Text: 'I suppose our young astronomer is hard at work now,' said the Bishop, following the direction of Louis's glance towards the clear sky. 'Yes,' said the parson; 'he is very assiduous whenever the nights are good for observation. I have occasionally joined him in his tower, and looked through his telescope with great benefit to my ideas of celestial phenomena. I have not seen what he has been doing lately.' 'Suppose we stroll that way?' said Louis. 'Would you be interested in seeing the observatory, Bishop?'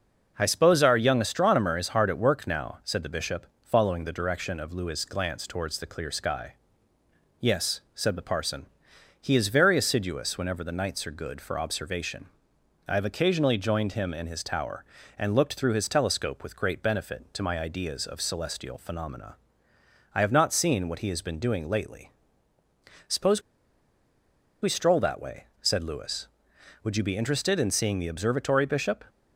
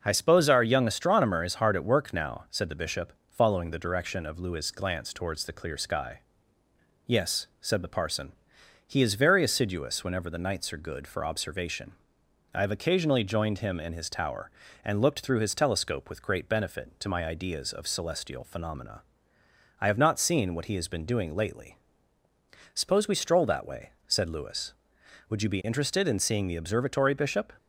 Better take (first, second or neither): second